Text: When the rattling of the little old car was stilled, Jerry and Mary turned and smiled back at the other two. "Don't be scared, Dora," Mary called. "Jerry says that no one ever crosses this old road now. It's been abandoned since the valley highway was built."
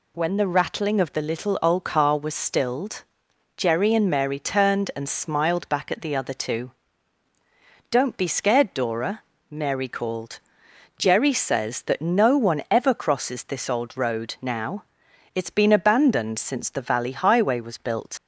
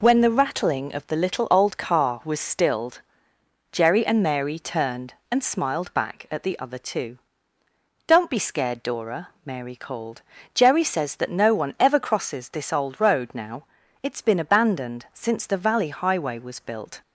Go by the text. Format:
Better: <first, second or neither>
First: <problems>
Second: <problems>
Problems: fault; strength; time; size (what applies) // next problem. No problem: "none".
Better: second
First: leaves "built" unfinished; at 18.1 s; 60 ms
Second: none